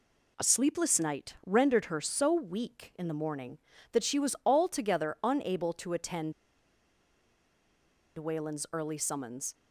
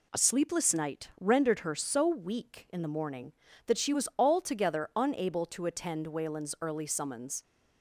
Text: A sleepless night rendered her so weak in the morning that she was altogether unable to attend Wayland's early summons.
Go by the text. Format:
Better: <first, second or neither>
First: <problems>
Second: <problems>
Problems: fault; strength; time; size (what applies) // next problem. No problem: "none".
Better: second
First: pauses between "attend" and "Wayland's"; strong; at 6.3 s; 1.8 s long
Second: none